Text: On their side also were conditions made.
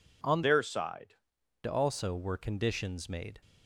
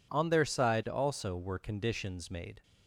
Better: second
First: changes voice from "their" to "side"; from 0.4 to 1.1 s; 0.7 s long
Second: none

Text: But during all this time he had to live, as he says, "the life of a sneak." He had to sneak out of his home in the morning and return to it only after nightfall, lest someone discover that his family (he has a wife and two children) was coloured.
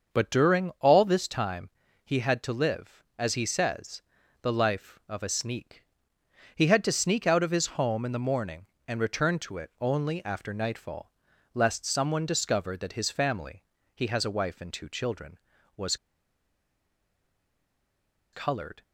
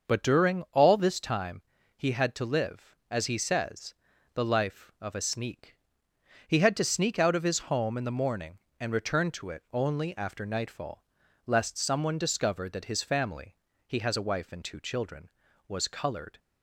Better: second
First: starts louder than the rest; until 1.2 s; 6.5 dB // pauses between "time" and "he"; slight; at 1.6 s; 0.34 s long // pauses between "was" and "coloured"; strong; at 15.9 s; 2.3 s long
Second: starts louder than the rest; until 1.1 s; 6.5 dB // pauses between "time" and "he"; slight; at 1.6 s; 0.34 s long

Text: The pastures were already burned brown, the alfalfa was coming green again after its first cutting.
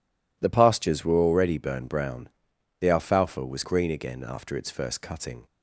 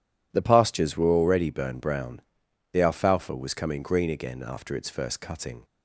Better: second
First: skips "coming"; at 3.6 s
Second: none

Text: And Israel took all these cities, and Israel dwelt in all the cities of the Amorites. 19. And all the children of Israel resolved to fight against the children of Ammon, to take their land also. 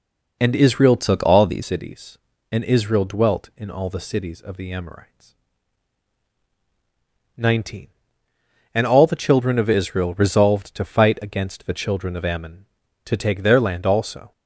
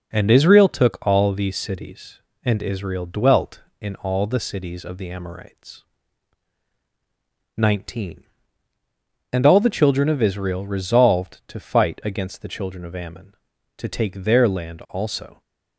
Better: second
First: changes voice from "took" to "these"; from 0.9 to 1.6 s; 0.7 s long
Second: none

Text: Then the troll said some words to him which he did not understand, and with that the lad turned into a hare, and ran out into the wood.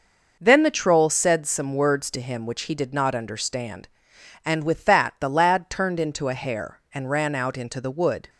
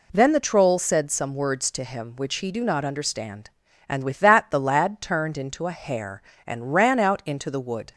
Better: first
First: none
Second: says "do" for "did"; at 2.5 s

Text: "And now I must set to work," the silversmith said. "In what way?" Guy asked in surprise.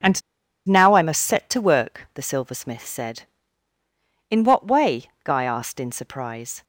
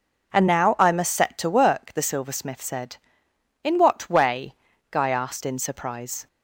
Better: second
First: pauses between "And" and "now"; noticeable; at 0.2 s; 0.48 s long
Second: none

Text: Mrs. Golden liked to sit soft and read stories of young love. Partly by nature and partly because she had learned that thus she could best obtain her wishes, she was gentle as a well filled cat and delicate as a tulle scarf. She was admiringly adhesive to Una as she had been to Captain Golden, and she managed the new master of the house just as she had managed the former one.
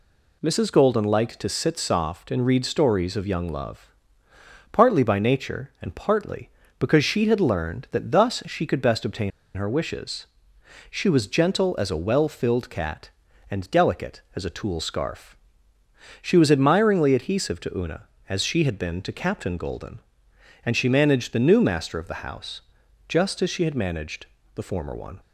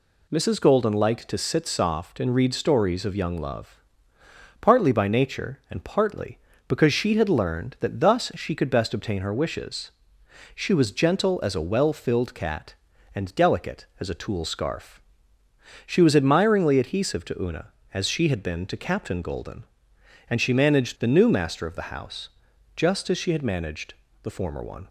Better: second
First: pauses between "obtain" and "her"; slight; at 9.3 s; 0.26 s long // pauses between "house" and "just"; noticeable; at 22.6 s; 0.48 s long // pauses between "managed" and "the"; slight; at 24.2 s; 0.28 s long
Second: pauses between "house" and "just"; noticeable; at 22.2 s; 0.48 s long // pauses between "managed" and "the"; slight; at 23.9 s; 0.28 s long

